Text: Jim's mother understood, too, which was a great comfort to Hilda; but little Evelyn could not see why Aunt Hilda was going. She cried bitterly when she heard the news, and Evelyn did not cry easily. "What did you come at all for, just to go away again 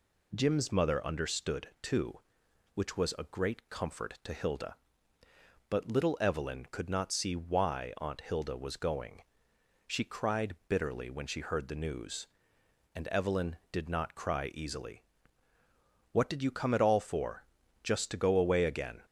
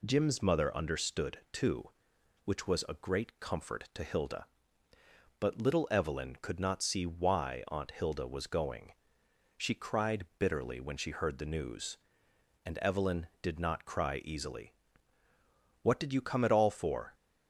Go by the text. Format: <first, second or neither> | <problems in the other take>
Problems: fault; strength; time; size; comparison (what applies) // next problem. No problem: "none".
first | stops before "just to go away again"; at 17.1 s